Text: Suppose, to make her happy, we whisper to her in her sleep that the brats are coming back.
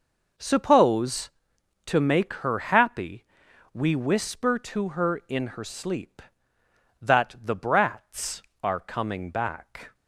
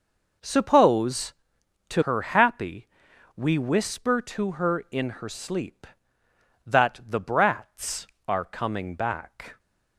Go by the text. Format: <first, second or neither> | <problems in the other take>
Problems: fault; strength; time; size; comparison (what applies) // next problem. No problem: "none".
first | skips "make"; at 2.0 s